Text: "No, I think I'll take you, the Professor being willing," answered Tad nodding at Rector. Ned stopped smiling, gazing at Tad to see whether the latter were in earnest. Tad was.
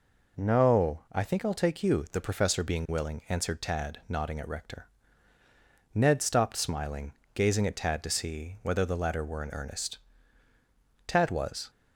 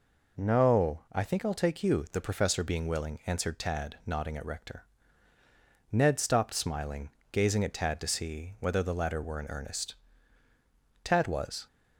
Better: neither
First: none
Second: none

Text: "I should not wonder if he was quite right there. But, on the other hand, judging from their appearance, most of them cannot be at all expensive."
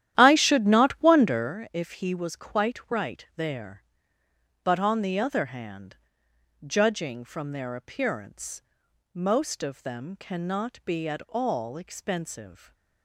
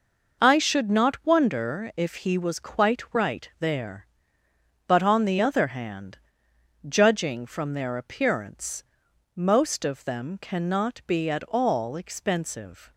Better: second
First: starts louder than the rest; strong; until 1.5 s; 11.5 dB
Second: none

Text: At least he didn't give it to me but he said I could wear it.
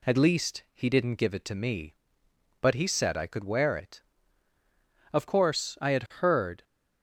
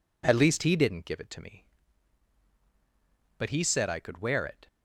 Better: second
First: goes on to say "Of course I had heard"; from 5.1 s on; 1.5 s long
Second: none

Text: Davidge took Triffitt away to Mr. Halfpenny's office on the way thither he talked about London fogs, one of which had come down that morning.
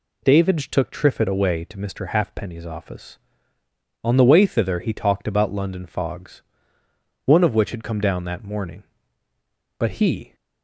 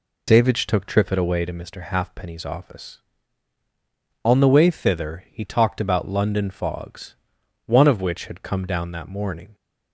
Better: second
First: goes on to say "But he"; from 9.7 s on; 0.56 s long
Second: none

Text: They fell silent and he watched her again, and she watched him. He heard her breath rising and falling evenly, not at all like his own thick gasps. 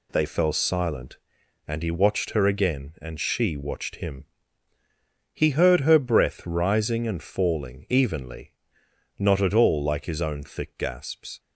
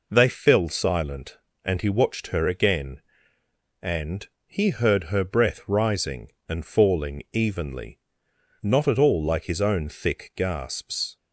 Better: first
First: none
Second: skips "she watched him"; at 4.3 s

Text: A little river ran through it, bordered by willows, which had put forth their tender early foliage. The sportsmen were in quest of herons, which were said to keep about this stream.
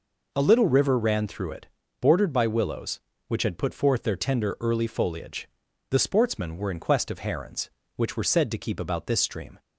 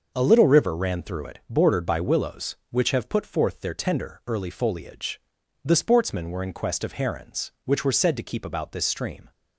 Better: first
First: none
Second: says "have" for "had"; at 2.9 s

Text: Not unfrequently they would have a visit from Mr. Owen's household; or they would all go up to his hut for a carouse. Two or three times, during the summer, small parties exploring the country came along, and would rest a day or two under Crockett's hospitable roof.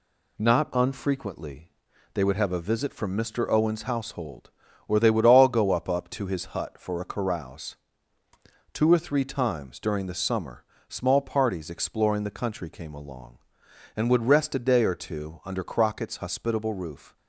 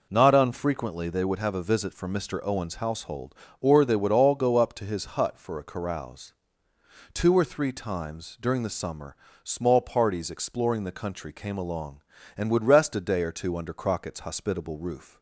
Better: second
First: pauses between "unfrequently" and "they"; at 1.7 s; 0.42 s long // says "up" twice; at 5.8 s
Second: none

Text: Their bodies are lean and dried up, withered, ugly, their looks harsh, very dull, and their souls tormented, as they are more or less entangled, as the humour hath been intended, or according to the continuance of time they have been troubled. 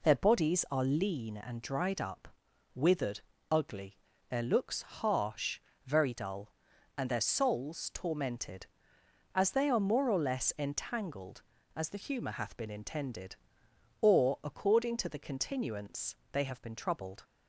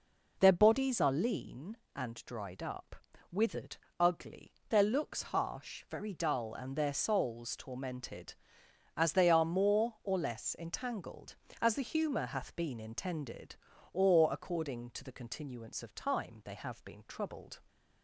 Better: second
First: skips "of time"; at 16.2 s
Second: none

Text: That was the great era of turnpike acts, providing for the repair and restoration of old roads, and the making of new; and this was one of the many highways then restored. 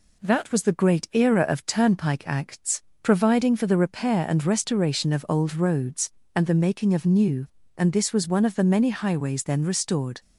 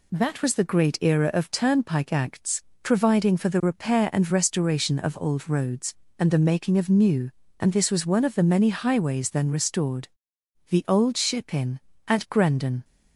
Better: first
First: none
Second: goes on to say "The Old Ship inn at Grendon"; strong; from 10.6 s on; 2.1 s long

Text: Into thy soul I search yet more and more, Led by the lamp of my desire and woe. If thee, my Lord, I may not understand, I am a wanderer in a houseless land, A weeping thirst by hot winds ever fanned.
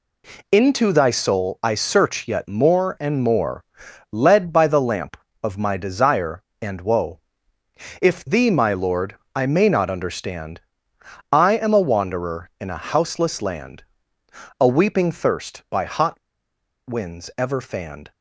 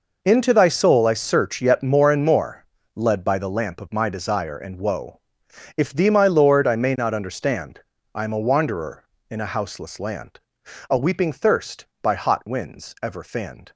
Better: second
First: pauses between "hot" and "winds"; noticeable; at 16.1 s; 0.68 s long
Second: none

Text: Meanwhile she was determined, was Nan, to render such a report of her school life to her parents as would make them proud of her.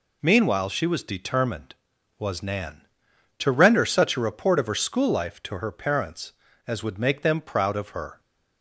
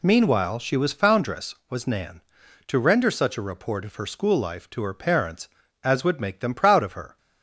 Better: first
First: none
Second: says "foundress" for "determined"; at 0.9 s

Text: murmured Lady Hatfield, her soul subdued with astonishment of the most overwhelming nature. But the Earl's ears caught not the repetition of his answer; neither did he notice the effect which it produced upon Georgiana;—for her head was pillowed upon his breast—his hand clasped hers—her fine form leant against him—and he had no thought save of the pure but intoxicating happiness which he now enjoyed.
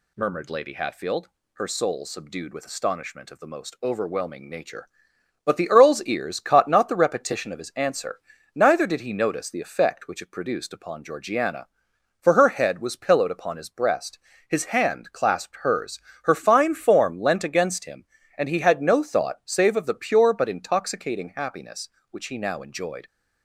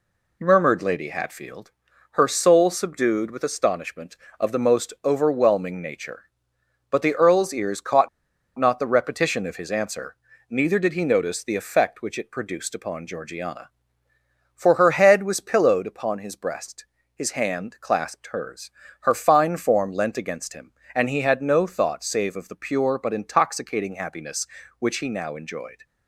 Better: first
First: none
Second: pauses between "caught" and "not"; noticeable; at 8.0 s; 0.50 s long

